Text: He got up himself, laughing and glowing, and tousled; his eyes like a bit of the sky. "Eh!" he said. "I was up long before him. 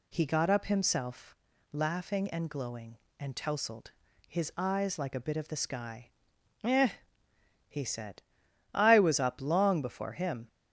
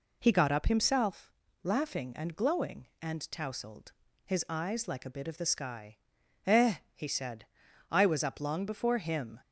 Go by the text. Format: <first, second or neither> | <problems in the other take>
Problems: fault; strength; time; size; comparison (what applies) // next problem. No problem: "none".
neither | none